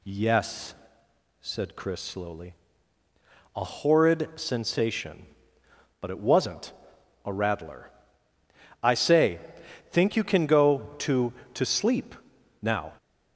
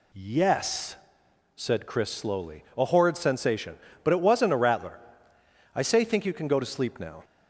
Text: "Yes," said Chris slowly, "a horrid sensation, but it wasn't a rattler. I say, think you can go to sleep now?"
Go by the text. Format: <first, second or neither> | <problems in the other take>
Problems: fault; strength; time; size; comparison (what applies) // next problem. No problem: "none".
second | pauses between "wasn't" and "a"; noticeable; at 6.7 s; 0.52 s long // says "to" twice; at 11.5 s // pauses between "sleep" and "now"; noticeable; at 12.1 s; 0.46 s long